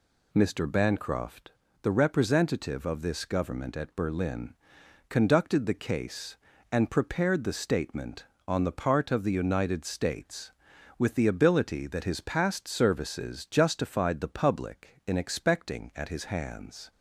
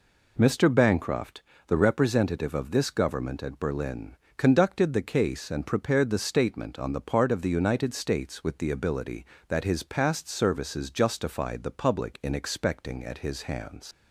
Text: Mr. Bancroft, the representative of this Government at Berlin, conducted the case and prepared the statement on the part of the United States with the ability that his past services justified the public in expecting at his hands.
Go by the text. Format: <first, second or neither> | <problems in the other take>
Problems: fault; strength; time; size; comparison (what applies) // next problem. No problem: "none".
first | leaves "hands" unfinished; at 13.9 s; 95 ms